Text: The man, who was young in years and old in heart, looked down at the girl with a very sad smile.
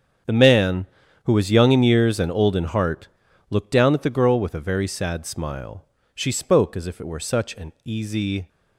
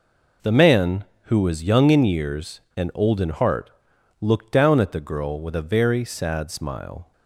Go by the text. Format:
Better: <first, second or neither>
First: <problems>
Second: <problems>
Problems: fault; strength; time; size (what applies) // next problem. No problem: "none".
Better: second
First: starts louder than the rest; strong; until 1.6 s; 7.5 dB // goes on to say "She spoke as if it were such an easy"; strong; from 6.1 s on; 2.3 s long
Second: none